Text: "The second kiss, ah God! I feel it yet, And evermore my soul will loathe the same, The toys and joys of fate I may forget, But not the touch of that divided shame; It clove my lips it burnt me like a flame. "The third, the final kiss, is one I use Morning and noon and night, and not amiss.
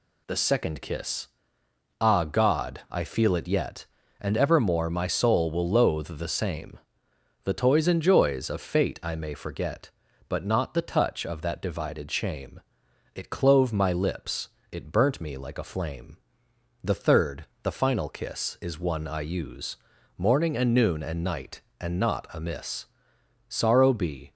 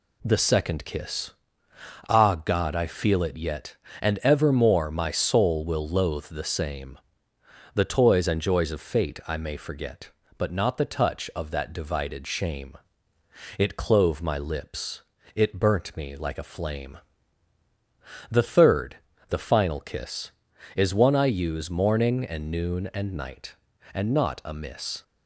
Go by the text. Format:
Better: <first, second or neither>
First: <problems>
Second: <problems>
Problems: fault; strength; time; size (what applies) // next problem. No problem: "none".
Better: second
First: pauses between "lips" and "it"; slight; at 14.4 s; 0.24 s long // pauses between "use" and "Morning"; at 19.7 s; 0.40 s long // goes on to say "Sorrow be"; noticeable; from 23.5 s on; 0.82 s long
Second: pauses between "lips" and "it"; slight; at 15.0 s; 0.34 s long